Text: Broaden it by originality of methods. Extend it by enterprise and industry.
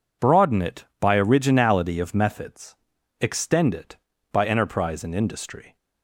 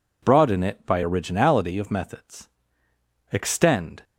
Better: first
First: none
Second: stops before "it by enterprise and industry"; at 4.0 s

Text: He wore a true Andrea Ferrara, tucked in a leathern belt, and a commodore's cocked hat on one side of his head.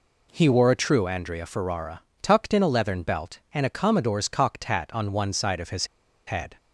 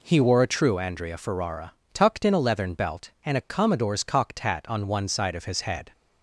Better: second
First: pauses between "his" and "head"; at 5.8 s; 0.40 s long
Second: none

